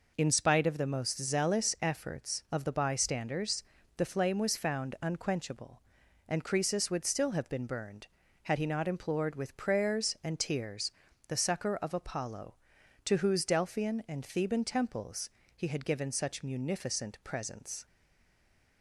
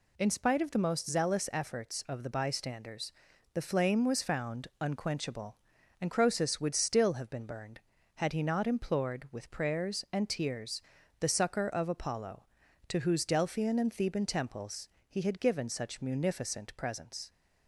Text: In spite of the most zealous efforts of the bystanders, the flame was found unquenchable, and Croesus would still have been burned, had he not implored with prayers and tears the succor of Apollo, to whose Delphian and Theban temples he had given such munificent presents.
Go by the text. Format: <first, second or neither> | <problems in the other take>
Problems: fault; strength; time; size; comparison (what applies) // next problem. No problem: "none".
second | pauses between "tears" and "the"; slight; at 10.9 s; 0.36 s long; also in the second // pauses between "temples" and "he"; slight; at 15.2 s; 0.26 s long; slight in the second // stays silent after the last word; slight; from 17.8 s on; 1.0 s long